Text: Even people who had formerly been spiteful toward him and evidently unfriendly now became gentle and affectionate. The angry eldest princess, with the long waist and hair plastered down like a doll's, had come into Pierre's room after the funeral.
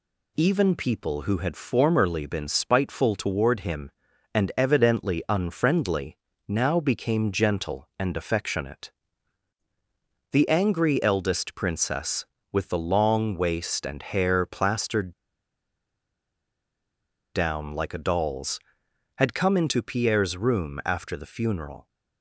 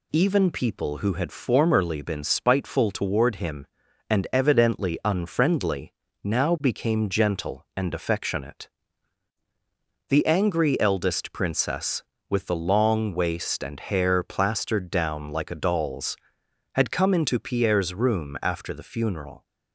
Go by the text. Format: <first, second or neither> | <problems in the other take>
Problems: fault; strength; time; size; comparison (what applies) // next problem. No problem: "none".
second | pauses between "unfriendly" and "now"; slight; at 6.1 s; 0.30 s long; slight in the second // pauses between "plastered" and "down"; strong; at 15.1 s; 2.2 s long